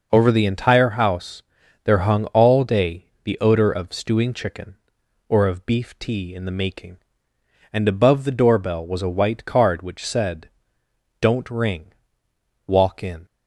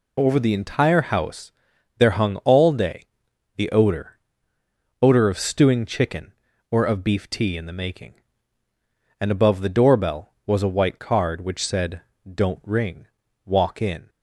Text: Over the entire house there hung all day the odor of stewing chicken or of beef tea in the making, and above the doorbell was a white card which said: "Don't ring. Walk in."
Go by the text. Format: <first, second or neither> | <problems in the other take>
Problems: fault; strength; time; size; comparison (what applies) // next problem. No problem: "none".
first | pauses between "house" and "there"; noticeable; at 1.5 s; 0.46 s long; also in the first // pauses between "day" and "the"; noticeable; at 3.0 s; 0.52 s long; slight in the first // says "odor" twice; at 5.0 s